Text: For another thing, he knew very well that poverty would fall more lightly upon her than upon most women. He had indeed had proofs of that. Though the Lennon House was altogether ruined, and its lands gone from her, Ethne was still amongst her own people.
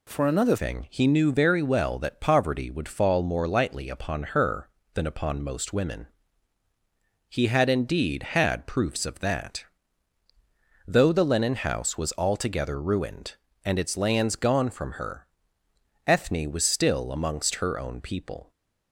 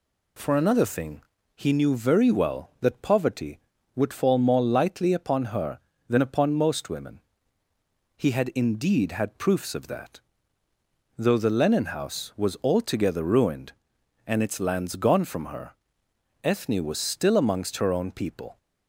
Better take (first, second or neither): second